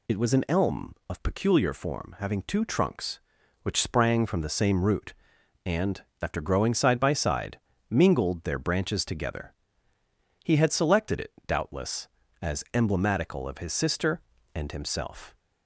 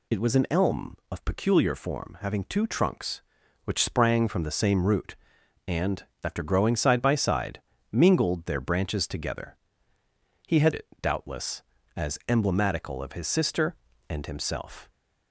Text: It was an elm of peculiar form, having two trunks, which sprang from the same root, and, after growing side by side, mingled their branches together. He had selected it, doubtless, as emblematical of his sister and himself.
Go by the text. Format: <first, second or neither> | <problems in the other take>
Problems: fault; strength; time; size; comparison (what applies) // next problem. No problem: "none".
first | skips "selected"; at 10.7 s